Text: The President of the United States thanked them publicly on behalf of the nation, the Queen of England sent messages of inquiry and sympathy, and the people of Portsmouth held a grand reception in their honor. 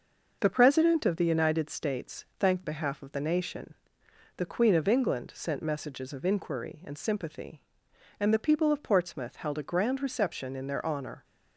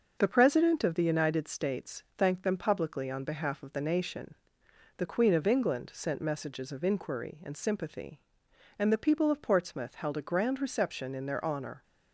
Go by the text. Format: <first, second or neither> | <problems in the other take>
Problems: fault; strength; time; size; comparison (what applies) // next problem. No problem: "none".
second | skips "them publicly on"; at 2.6 s